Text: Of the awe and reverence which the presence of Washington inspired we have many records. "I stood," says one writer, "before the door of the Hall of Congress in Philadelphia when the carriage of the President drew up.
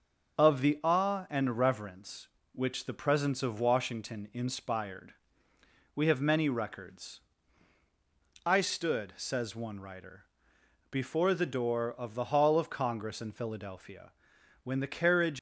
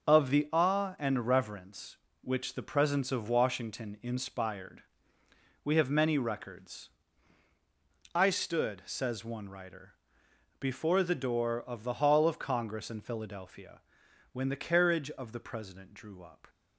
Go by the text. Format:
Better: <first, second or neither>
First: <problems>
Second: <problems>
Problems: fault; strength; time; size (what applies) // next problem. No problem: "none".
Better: second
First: starts louder than the rest; noticeable; until 1.4 s; 6 dB // pauses between "inspired" and "we"; noticeable; at 5.1 s; 0.80 s long // pauses between "Philadelphia" and "when"; noticeable; at 14.1 s; 0.50 s long // stops before "of the President drew up"; at 15.3 s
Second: starts louder than the rest; noticeable; until 1.1 s; 6 dB // pauses between "inspired" and "we"; noticeable; at 4.8 s; 0.80 s long // pauses between "Philadelphia" and "when"; noticeable; at 13.8 s; 0.50 s long